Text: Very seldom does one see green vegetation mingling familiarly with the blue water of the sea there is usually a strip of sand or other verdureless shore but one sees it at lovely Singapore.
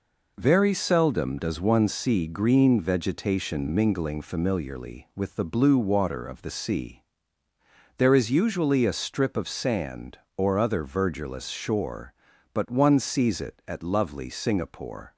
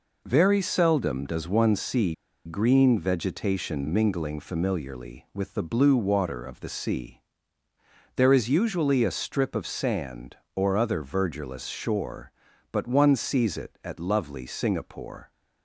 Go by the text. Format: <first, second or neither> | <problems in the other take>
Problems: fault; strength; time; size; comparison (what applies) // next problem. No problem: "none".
first | pauses between "see" and "green"; slight; at 2.1 s; 0.31 s long // pauses between "sea" and "there"; noticeable; at 7.2 s; 0.96 s long; noticeable in the first